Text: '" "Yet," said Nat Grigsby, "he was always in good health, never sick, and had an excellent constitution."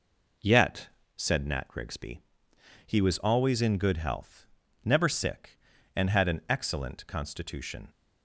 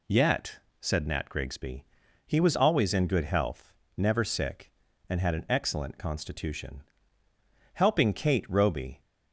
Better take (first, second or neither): first